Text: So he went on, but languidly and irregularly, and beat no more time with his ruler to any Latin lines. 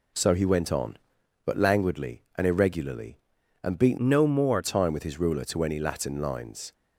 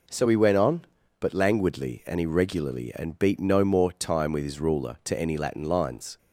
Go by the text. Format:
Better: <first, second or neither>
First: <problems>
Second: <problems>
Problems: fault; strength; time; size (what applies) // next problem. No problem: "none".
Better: second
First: changes voice from "no" to "more"; from 3.9 to 4.6 s; 0.7 s long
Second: none